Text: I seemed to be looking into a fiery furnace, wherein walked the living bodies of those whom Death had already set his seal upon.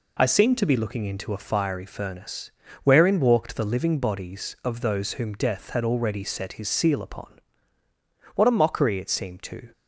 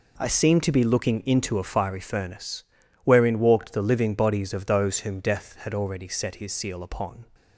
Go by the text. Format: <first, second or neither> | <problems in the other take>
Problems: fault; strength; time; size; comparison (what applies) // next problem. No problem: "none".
second | goes on to say "What a mockery it seemed to"; from 8.3 s on; 1.3 s long